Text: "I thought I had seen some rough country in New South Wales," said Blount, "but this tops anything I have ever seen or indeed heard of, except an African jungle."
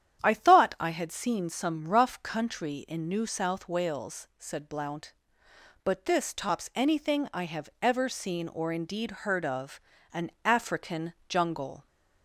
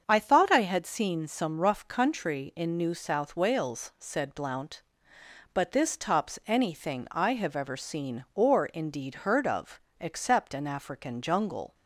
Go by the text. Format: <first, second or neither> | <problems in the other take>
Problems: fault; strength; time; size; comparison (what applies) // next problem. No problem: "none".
second | starts louder than the rest; strong; until 1.2 s; 9.5 dB; strong in the second // skips "except"; at 9.9 s // pauses between "African" and "jungle"; slight; at 11.1 s; 0.16 s long